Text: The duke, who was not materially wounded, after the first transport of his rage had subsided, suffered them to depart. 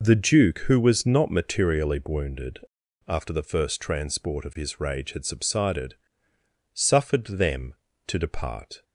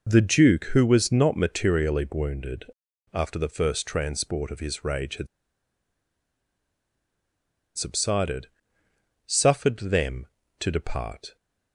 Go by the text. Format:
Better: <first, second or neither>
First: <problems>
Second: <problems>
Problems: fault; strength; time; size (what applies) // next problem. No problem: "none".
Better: first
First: none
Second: pauses between "had" and "subsided"; strong; at 5.2 s; 2.4 s long